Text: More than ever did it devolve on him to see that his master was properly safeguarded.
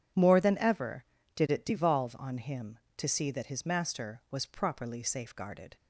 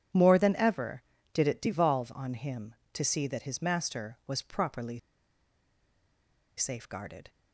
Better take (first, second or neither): first